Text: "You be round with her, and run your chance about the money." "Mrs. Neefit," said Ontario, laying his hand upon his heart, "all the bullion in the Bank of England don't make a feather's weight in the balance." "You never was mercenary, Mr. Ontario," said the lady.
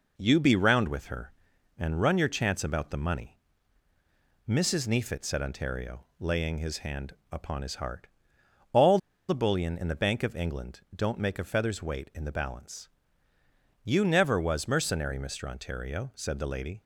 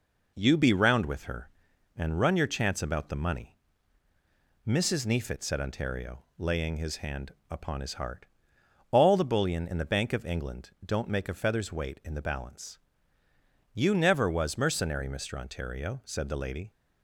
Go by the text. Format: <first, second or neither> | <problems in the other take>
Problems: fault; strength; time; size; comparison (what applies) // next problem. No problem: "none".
second | pauses between "hand" and "upon"; slight; at 7.1 s; 0.18 s long; slight in the second // pauses between "all" and "the"; slight; at 8.9 s; 0.30 s long